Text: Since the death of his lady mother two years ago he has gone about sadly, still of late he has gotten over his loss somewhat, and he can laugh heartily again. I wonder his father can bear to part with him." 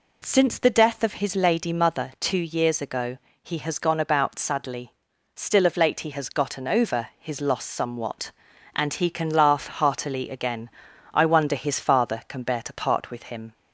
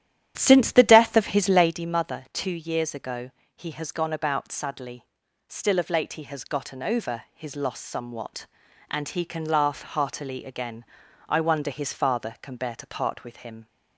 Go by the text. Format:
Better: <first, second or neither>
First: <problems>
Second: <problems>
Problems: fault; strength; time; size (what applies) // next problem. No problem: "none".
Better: first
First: pauses between "ago" and "he"; slight; at 3.1 s; 0.26 s long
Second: starts louder than the rest; strong; until 1.8 s; 10.5 dB // pauses between "ago" and "he"; slight; at 3.3 s; 0.26 s long